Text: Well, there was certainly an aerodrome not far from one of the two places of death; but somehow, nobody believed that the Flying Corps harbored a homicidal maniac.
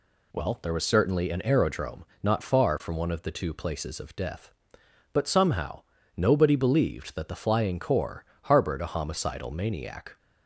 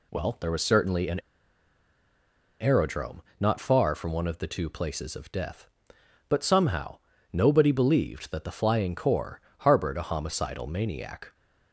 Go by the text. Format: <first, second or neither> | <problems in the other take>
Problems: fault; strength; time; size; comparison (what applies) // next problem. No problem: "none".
first | pauses between "an" and "aerodrome"; strong; at 1.1 s; 1.4 s long // pauses between "aerodrome" and "not"; slight; at 3.2 s; 0.18 s long; slight in the first // pauses between "Corps" and "harbored"; slight; at 9.3 s; 0.18 s long; slight in the first